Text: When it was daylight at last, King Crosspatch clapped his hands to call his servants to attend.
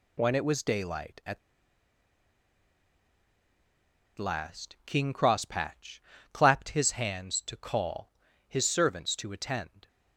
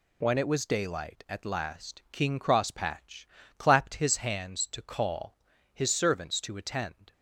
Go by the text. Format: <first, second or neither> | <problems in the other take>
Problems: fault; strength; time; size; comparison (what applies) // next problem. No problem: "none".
second | pauses between "at" and "last"; strong; at 1.3 s; 2.7 s long // pauses between "Crosspatch" and "clapped"; slight; at 5.9 s; 0.32 s long; slight in the second // pauses between "call" and "his"; slight; at 8.1 s; 0.34 s long; slight in the second